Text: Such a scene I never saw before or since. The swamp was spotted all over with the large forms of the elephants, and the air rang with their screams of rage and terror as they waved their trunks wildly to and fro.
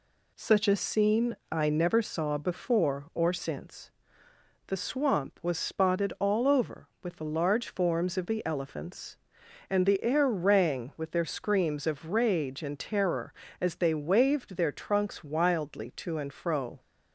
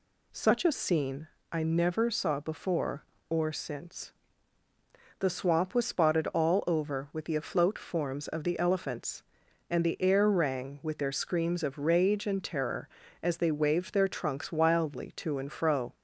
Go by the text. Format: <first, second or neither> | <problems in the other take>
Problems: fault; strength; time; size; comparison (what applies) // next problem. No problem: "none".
first | pauses between "scene" and "I"; slight; at 1.2 s; 0.26 s long; slight in the first // says "afloat" for "large"; at 7.3 s